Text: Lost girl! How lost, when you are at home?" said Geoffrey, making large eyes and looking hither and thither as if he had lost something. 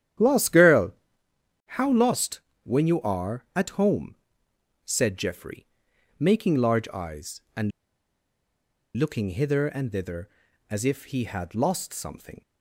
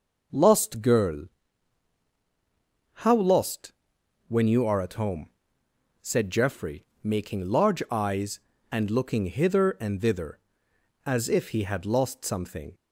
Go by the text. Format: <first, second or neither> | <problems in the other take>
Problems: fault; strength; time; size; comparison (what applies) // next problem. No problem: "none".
second | starts louder than the rest; strong; until 2.0 s; 11 dB // pauses between "and" and "looking"; strong; at 7.7 s; 1.2 s long